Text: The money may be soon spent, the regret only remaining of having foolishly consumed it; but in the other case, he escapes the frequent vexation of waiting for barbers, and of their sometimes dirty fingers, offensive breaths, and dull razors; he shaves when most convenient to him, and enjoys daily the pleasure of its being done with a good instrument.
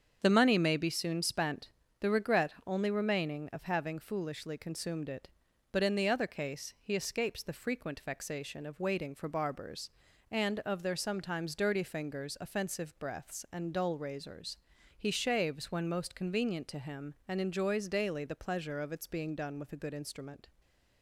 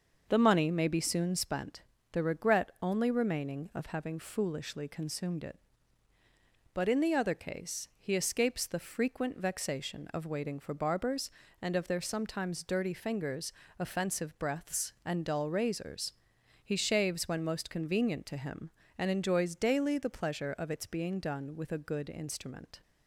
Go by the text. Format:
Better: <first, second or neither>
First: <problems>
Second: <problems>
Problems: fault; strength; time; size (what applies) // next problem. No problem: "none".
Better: neither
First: starts louder than the rest; strong; until 1.2 s; 7.5 dB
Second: starts louder than the rest; noticeable; until 1.2 s; 6 dB